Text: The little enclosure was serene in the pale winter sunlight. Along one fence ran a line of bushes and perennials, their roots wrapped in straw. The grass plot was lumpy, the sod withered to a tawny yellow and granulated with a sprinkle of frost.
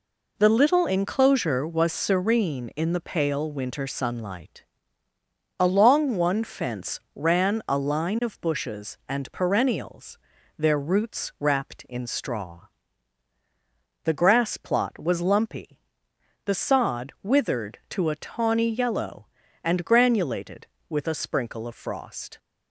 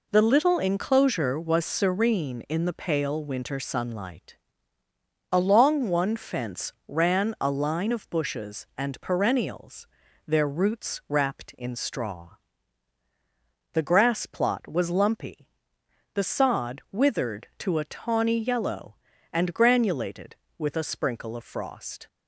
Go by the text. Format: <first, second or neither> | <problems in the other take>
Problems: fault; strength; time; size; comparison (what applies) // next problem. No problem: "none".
neither | none